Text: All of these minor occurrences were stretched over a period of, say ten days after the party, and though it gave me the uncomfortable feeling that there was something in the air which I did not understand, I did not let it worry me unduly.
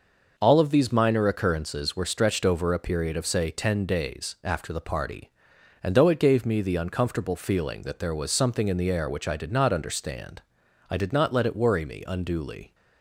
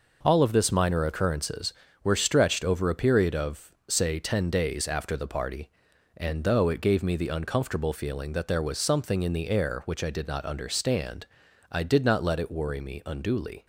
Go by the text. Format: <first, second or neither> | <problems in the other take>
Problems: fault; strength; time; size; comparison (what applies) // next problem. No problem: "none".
first | says "this" for "these"; at 0.5 s